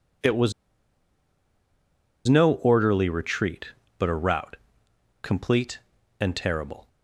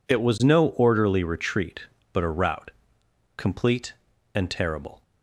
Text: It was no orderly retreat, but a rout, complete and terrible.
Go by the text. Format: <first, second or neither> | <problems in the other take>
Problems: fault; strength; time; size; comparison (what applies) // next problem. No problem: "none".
second | pauses between "was" and "no"; strong; at 0.5 s; 1.7 s long